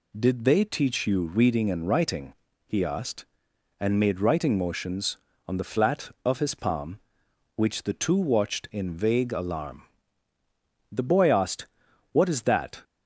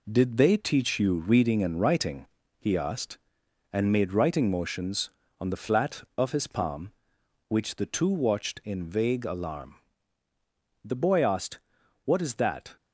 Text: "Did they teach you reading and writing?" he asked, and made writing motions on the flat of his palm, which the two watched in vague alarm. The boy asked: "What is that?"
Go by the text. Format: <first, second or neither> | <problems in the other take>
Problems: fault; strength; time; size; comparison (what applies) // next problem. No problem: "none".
first | gets quieter; noticeable; throughout; 5.5 dB